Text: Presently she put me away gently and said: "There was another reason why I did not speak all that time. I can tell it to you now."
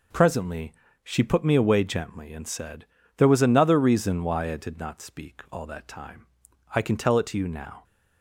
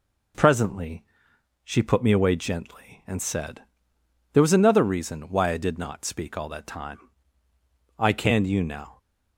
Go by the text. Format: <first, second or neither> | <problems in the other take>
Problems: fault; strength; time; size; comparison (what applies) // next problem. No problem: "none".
first | pauses between "Presently" and "she"; noticeable; at 1.0 s; 0.62 s long; slight in the first // skips "tell it to"; at 8.4 s